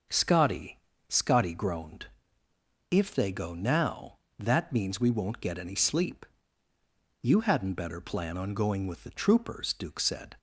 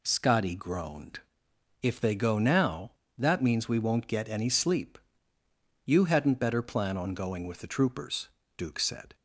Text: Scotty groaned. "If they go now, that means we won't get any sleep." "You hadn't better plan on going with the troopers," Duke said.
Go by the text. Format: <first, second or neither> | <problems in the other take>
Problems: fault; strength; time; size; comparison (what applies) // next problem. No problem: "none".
second | starts louder than the rest; until 1.4 s; 6 dB // says "Scotty" twice; at 1.1 s